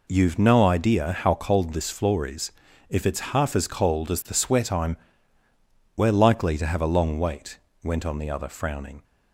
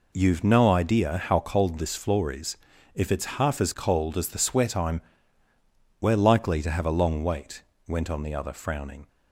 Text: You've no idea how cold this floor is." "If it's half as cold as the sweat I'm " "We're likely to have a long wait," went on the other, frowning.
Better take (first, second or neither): neither